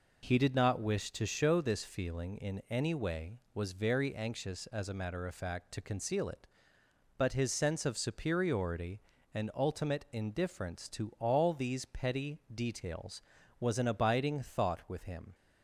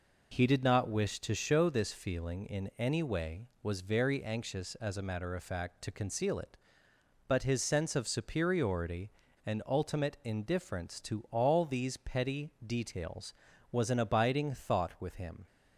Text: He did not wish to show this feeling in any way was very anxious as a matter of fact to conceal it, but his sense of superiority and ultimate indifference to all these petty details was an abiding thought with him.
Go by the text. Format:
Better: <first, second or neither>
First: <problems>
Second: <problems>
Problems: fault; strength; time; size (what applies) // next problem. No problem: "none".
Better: neither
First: pauses between "petty" and "details"; slight; at 12.3 s; 0.16 s long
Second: pauses between "petty" and "details"; slight; at 12.5 s; 0.16 s long